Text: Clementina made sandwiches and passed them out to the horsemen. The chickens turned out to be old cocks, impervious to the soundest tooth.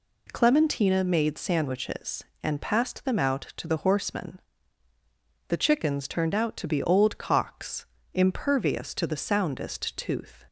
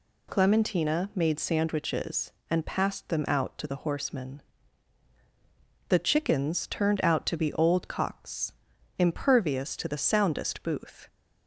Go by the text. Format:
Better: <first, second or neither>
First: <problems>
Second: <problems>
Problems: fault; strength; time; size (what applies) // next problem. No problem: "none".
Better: first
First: none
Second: says "booth" for "tooth"; at 10.6 s